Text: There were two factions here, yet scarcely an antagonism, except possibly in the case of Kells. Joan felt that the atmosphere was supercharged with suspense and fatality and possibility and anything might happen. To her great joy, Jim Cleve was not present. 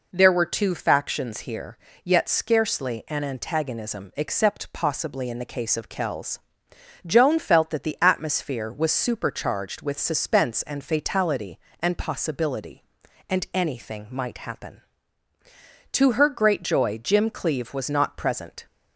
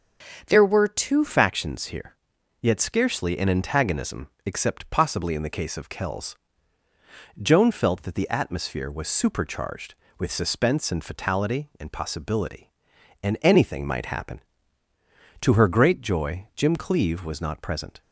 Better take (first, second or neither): first